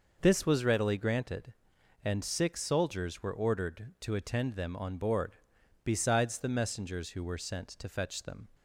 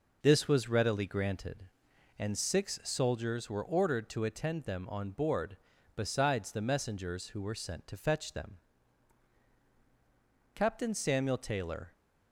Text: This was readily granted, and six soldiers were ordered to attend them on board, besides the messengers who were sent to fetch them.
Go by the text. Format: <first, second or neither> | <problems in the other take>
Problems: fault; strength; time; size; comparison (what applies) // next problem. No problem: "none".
first | goes on to say "Captain Samuel Taylor"; from 10.5 s on; 1.3 s long